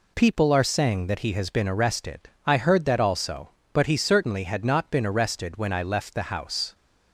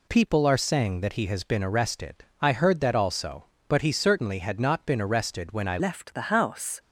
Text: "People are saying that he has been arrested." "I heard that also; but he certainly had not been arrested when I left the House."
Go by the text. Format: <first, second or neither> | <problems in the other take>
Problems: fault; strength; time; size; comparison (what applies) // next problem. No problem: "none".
first | changes voice at "left"; from 5.8 s on; 0.9 s long